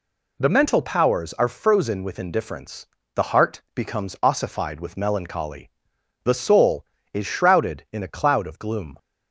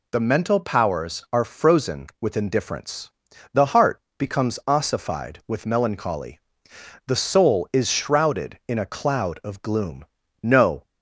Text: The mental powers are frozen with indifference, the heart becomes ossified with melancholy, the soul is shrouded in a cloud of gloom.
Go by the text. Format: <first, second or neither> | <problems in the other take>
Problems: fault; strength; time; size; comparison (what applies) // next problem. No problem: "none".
first | pauses between "heart" and "becomes"; slight; at 3.9 s; 0.18 s long // goes on to say "No"; slight; from 10.4 s on; 0.40 s long